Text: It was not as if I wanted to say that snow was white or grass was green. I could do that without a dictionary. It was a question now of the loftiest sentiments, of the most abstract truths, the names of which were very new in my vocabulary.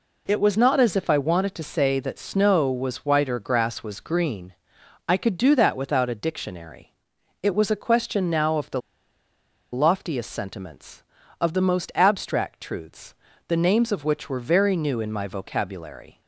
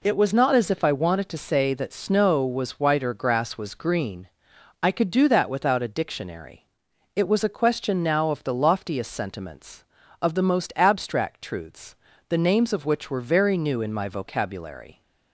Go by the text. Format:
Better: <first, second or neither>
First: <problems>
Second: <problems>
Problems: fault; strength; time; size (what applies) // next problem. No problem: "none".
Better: second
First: pauses between "the" and "loftiest"; noticeable; at 8.8 s; 0.92 s long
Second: none